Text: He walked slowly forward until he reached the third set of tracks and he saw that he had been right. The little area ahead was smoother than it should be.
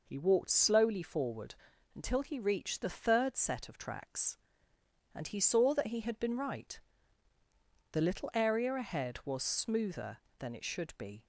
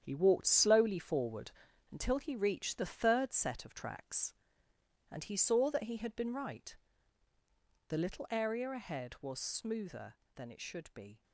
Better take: first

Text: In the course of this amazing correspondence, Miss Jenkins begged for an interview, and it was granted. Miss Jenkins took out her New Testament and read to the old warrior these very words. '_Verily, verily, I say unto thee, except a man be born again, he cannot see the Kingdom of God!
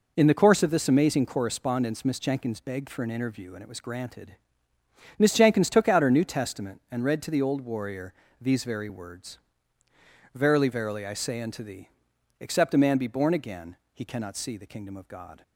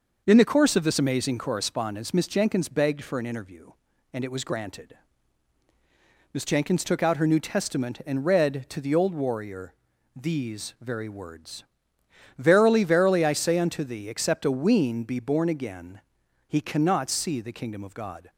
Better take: first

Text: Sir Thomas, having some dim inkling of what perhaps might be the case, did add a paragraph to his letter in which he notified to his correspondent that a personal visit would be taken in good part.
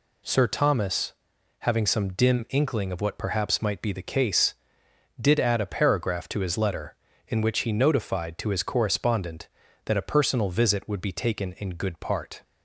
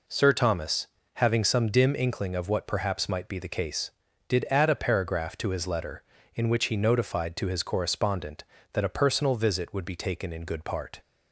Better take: neither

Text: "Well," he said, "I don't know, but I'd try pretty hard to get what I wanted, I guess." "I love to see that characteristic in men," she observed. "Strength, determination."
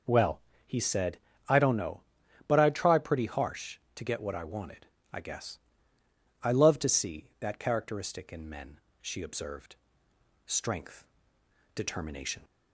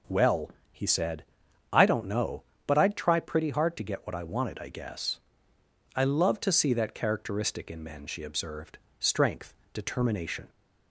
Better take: second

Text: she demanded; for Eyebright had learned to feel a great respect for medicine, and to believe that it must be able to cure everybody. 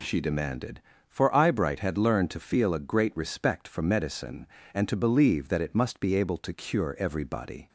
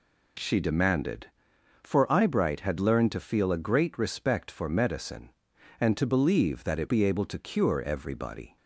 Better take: first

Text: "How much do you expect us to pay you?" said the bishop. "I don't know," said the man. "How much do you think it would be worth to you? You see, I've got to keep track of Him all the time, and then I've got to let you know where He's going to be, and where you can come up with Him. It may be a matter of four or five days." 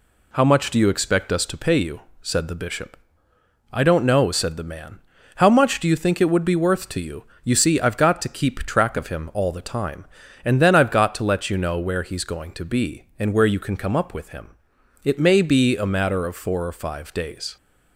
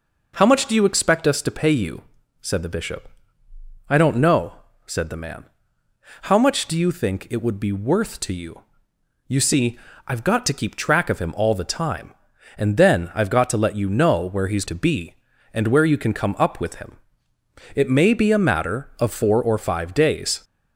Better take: first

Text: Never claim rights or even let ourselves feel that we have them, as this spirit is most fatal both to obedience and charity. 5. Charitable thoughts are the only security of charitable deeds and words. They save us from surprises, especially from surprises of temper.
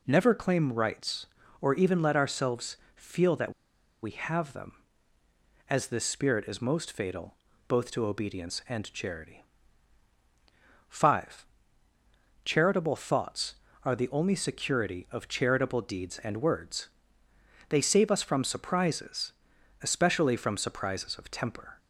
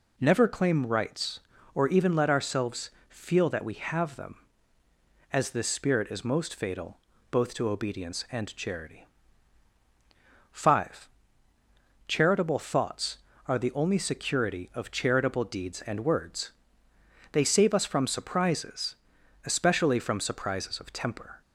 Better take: second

